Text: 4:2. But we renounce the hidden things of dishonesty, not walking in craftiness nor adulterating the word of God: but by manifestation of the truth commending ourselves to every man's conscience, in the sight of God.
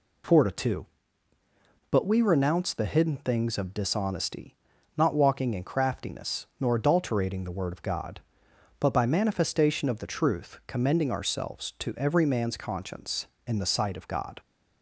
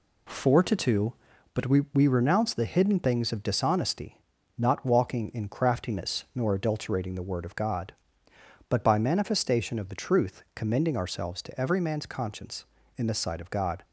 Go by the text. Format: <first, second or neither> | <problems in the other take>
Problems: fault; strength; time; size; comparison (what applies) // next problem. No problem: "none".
first | says "we" twice; at 1.9 s